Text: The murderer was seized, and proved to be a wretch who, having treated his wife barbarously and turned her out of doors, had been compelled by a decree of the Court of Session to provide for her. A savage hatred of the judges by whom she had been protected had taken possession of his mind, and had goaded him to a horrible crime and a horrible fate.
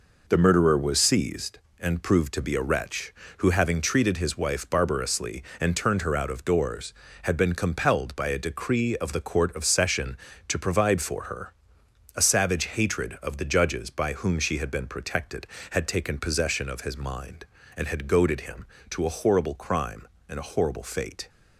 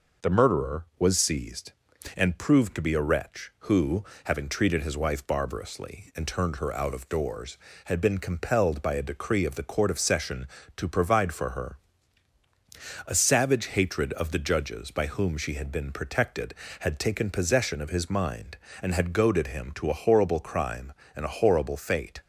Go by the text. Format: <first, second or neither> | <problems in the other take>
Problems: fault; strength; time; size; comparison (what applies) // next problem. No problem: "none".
neither | none